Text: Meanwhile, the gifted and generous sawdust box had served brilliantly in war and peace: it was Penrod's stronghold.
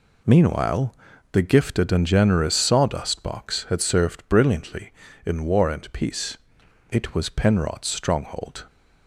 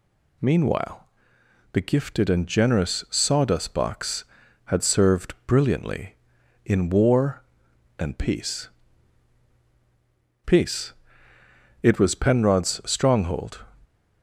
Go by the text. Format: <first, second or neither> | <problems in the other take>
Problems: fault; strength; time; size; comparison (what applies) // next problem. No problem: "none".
first | says "peace" twice; at 10.4 s